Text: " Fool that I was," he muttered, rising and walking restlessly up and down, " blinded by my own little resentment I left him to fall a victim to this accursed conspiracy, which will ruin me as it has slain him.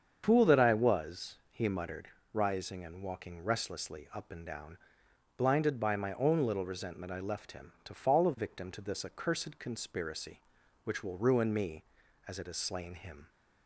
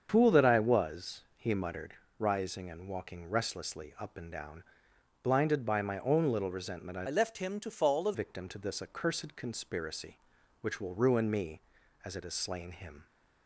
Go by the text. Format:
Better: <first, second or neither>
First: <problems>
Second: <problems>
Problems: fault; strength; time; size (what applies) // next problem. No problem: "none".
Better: first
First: starts louder than the rest; strong; until 1.2 s; 7.5 dB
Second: starts louder than the rest; strong; until 1.1 s; 7.5 dB // changes voice from "left" to "a"; from 7.0 to 8.1 s; 1.1 s long